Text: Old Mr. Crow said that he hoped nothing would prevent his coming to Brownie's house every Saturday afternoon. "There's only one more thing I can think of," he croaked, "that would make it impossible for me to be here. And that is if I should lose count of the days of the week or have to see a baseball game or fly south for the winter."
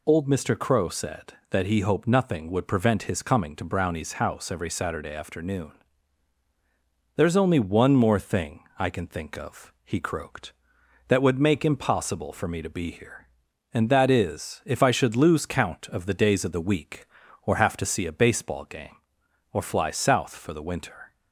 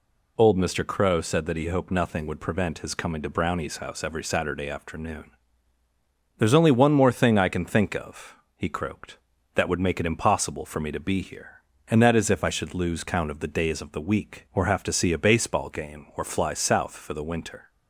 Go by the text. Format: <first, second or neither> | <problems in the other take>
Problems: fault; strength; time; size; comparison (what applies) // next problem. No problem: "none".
second | pauses between "thing" and "I"; slight; at 8.6 s; 0.16 s long // skips "it"; at 11.6 s